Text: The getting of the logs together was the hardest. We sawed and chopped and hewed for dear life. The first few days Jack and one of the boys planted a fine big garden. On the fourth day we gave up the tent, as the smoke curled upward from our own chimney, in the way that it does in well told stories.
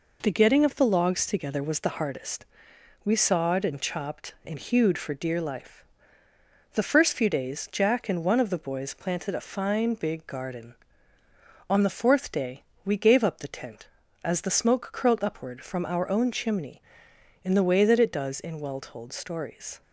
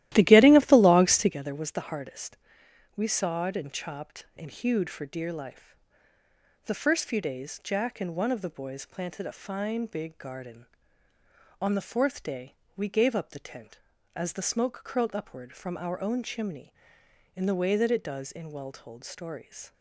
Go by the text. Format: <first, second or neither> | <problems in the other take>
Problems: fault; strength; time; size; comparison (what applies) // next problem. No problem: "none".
first | starts louder than the rest; strong; until 1.4 s; 14.5 dB // pauses between "day" and "we"; slight; at 12.5 s; 0.24 s long; slight in the first